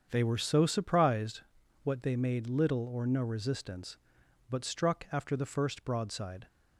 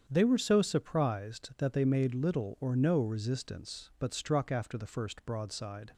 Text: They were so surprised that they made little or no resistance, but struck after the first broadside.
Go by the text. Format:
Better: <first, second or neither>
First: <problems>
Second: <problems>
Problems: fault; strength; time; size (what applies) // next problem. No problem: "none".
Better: second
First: starts louder than the rest; strong; until 1.1 s; 7.5 dB // says "what" for "that"; at 1.8 s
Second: starts louder than the rest; strong; until 1.0 s; 8 dB